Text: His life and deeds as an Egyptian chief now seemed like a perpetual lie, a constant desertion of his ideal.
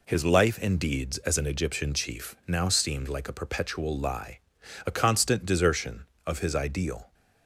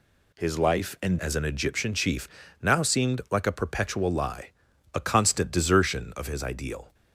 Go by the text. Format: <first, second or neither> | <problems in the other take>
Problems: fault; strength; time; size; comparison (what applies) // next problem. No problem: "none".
first | skips "deeds"; at 1.1 s // pauses between "chief" and "now"; slight; at 2.2 s; 0.34 s long